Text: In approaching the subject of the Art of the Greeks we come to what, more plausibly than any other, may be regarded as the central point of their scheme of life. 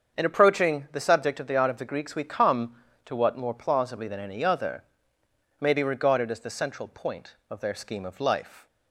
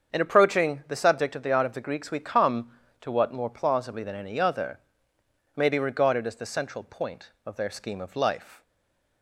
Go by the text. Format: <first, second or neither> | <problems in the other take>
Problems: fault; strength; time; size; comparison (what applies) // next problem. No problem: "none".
first | starts louder than the rest; until 1.1 s; 7 dB; also in the first // stays silent after the last word; slight; from 8.6 s on; 0.6 s long